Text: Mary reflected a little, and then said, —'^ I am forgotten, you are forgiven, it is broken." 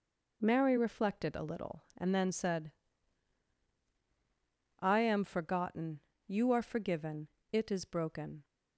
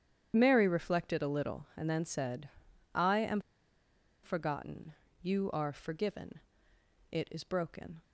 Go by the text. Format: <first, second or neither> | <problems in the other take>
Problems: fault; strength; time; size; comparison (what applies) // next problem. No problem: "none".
first | starts louder than the rest; strong; until 1.3 s; 9 dB // pauses between "am" and "forgotten"; noticeable; at 3.3 s; 0.84 s long